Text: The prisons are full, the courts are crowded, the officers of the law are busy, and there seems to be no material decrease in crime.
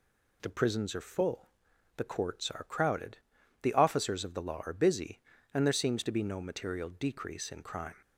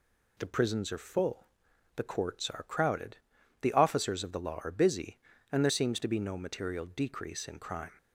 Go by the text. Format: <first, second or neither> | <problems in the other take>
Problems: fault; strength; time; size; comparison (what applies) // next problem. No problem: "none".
neither | none